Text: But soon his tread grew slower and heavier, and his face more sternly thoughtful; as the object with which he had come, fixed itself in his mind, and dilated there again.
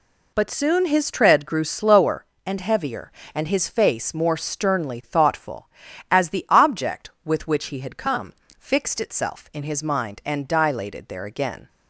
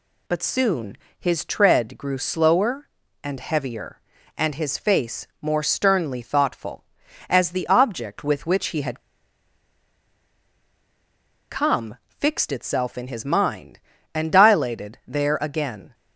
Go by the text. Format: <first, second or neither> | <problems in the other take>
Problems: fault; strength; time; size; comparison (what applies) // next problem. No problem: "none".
first | pauses between "soon" and "his"; slight; at 0.9 s; 0.22 s long // pauses between "had" and "come"; strong; at 8.9 s; 2.5 s long